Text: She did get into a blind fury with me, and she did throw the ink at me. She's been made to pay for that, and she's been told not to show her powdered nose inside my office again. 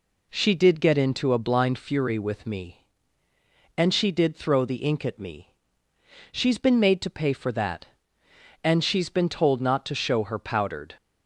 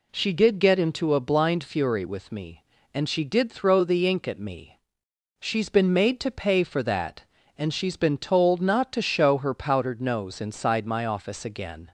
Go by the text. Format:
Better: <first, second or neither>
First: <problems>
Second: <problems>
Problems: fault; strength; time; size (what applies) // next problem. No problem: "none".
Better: second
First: stops before "nose inside my office again"; at 10.9 s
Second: none